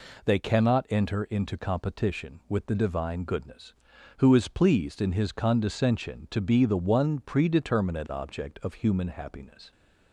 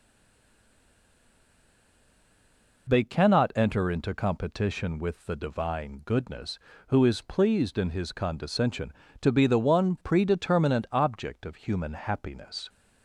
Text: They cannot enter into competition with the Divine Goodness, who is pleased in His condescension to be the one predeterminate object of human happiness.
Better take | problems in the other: first | stays silent before the first word; strong; until 2.8 s; 2.8 s long

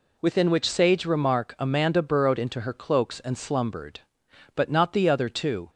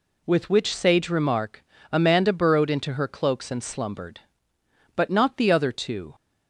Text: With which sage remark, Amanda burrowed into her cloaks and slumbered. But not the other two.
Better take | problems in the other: second | says "Within" for "With"; at 0.1 s

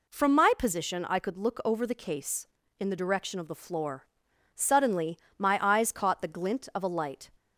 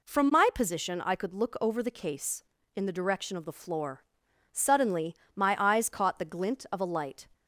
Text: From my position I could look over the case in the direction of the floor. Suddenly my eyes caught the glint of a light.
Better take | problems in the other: neither | pauses between "Suddenly" and "my"; slight; the same in both

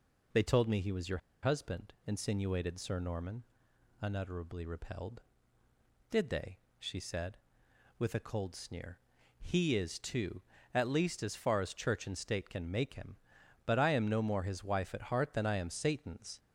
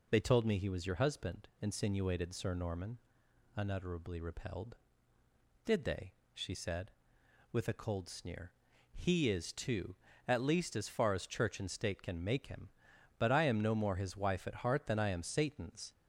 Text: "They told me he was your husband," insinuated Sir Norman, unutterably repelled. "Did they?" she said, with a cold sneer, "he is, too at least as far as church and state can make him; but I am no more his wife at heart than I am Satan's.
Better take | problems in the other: second | pauses between "your" and "husband"; slight; at 1.1 s; 0.24 s long

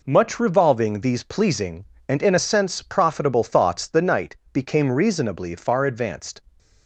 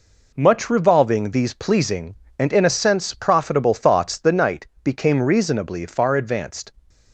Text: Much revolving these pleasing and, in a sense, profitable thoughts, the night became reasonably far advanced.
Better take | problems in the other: neither | pauses between "night" and "became"; slight; the same in both

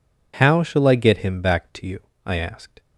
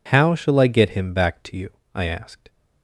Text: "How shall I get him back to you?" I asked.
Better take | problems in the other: neither | none

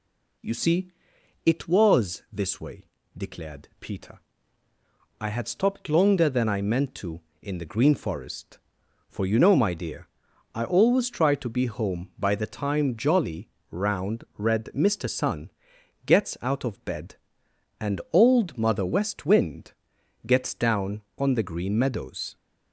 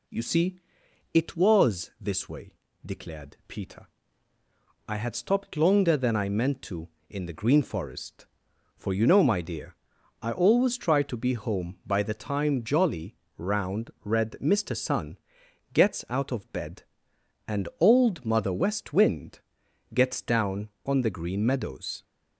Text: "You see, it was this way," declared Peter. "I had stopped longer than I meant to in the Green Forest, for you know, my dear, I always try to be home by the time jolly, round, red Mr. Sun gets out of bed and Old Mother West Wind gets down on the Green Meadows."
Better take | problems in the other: neither | pauses between "Sun" and "gets"; noticeable; the same in both // pauses between "Wind" and "gets"; noticeable; the same in both

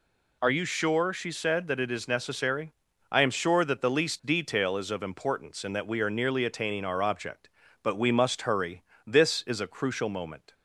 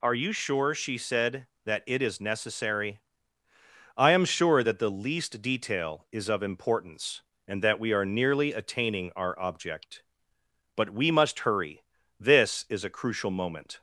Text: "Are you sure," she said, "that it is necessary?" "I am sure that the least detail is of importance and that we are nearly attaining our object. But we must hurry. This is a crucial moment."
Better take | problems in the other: neither | none

